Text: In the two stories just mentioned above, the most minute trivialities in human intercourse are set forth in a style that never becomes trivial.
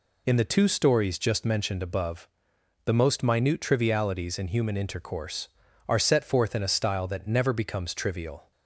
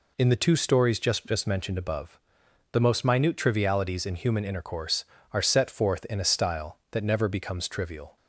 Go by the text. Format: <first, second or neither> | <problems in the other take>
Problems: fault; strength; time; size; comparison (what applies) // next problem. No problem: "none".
first | says "just" twice; at 1.2 s